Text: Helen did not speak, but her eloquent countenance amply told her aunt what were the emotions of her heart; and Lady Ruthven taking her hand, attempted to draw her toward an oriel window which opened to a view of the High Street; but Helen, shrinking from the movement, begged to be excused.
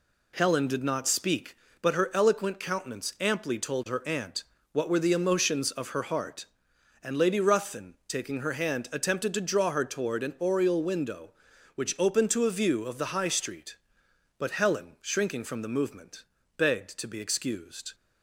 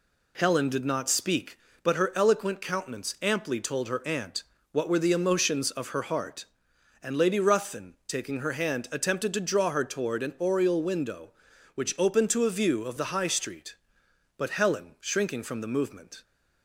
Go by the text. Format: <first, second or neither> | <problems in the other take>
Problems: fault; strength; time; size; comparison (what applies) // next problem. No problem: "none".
first | pauses between "aunt" and "what"; slight; at 4.4 s; 0.28 s long; slight in the first // stops before "begged to be excused"; at 16.2 s